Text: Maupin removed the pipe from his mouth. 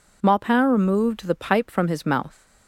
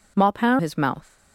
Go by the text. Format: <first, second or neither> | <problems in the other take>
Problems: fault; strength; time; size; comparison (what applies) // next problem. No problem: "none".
first | skips "removed the pipe from"; at 0.5 s